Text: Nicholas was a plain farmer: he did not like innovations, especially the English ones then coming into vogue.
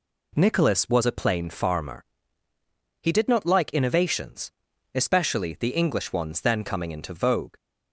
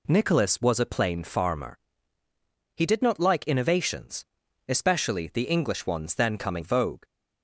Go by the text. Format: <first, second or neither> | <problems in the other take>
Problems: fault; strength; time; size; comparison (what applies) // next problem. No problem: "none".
first | skips "into"; at 6.6 s